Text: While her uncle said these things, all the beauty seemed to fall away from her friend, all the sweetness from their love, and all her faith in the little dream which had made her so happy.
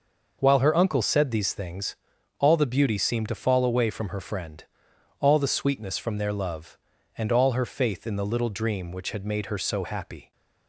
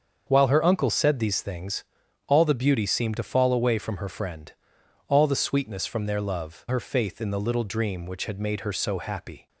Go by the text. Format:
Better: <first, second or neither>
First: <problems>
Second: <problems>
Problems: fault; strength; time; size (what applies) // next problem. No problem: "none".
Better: first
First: none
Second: starts louder than the rest; until 1.2 s; 6.5 dB // skips "and all"; at 6.6 s